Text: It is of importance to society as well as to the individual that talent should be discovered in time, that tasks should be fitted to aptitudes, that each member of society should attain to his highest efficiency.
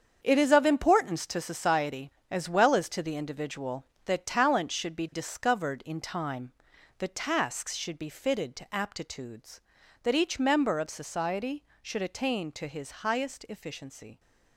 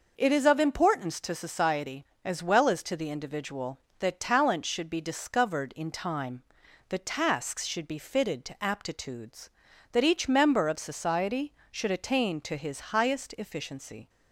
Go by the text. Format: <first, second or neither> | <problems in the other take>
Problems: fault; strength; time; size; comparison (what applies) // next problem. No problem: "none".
second | gets quieter; strong; throughout; 10 dB